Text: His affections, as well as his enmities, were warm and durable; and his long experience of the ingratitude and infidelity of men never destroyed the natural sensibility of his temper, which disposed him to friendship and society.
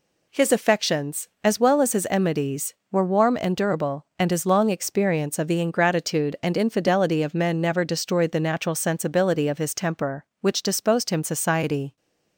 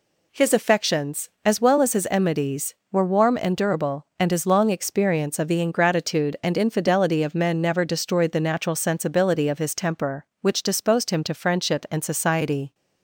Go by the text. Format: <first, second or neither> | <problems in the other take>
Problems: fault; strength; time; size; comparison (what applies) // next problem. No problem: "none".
second | skips "to friendship and"; at 11.2 s